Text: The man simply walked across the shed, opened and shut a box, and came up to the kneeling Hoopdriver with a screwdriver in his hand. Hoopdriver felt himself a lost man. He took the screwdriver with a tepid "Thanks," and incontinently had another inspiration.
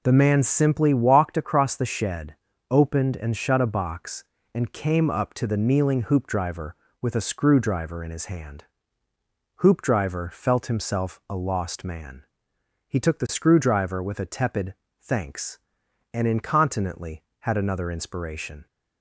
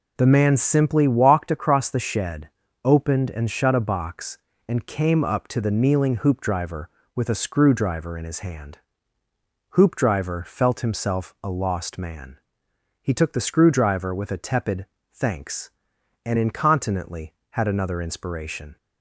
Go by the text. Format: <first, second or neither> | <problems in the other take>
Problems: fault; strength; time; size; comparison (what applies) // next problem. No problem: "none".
neither | pauses between "tepid" and "Thanks"; slight; the same in both